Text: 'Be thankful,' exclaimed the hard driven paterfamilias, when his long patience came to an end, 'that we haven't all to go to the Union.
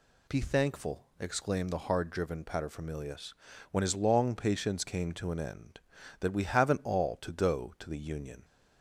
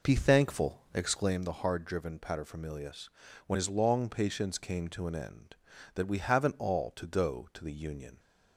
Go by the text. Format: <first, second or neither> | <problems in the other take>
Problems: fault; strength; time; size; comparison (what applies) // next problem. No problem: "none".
first | starts louder than the rest; noticeable; until 1.5 s; 4.5 dB